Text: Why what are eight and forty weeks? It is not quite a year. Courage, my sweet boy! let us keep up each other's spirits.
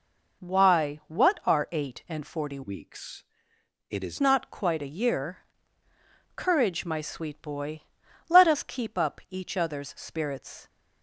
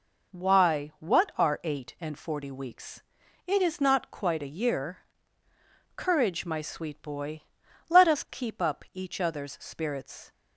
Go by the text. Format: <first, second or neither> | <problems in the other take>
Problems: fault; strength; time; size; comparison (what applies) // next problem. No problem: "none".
second | changes voice from "weeks" to "is"; from 2.6 to 4.1 s; 1.5 s long